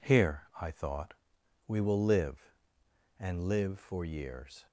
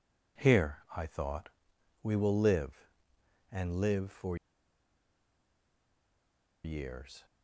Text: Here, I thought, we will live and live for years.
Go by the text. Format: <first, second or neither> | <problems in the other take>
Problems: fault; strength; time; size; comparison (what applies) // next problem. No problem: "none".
first | pauses between "for" and "years"; strong; at 4.3 s; 2.2 s long